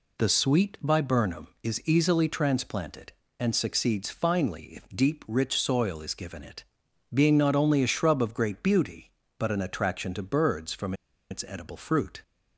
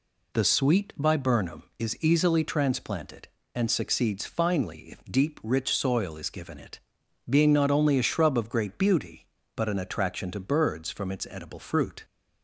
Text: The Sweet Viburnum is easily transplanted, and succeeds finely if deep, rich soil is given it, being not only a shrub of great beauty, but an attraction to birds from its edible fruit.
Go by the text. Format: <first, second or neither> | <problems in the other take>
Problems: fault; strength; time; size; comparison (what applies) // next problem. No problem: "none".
second | pauses between "from" and "its"; at 10.9 s; 0.36 s long